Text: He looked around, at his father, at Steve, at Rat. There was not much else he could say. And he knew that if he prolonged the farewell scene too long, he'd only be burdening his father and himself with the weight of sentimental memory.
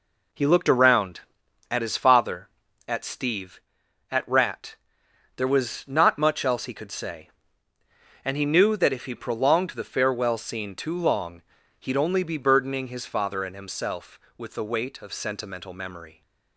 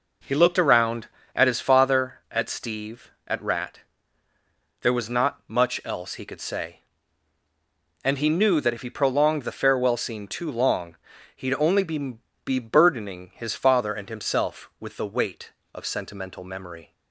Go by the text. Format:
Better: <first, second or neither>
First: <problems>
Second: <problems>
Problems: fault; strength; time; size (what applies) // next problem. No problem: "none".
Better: first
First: none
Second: says "be" twice; at 12.4 s